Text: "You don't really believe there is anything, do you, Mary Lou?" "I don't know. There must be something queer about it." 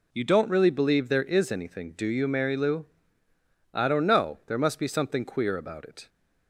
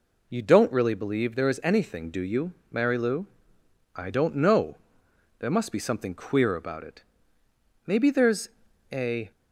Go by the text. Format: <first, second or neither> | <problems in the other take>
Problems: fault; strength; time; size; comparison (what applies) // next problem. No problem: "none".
first | goes on to say "Maybe there's a"; from 7.8 s on; 1.4 s long